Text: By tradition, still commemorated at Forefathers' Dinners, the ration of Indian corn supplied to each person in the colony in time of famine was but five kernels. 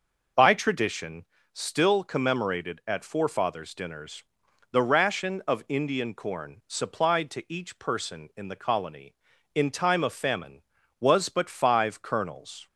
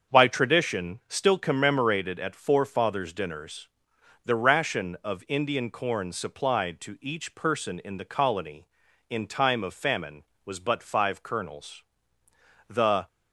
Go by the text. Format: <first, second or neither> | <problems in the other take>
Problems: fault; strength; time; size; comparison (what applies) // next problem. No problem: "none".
first | starts louder than the rest; until 1.1 s; 7 dB // goes on to say "The"; slight; from 12.6 s on; 0.38 s long